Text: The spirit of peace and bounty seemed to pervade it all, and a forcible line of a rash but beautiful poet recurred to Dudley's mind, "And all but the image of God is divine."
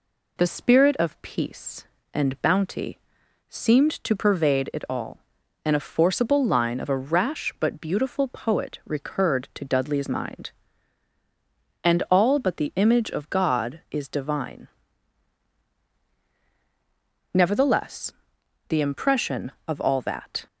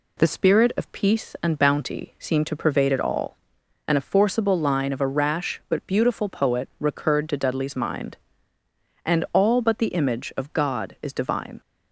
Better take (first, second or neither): second